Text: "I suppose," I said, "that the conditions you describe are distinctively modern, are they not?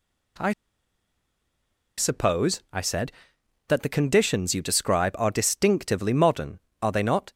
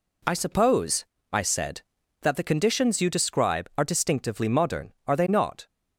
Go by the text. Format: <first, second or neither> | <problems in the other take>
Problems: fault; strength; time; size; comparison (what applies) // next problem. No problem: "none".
second | pauses between "I" and "suppose"; strong; at 0.5 s; 1.4 s long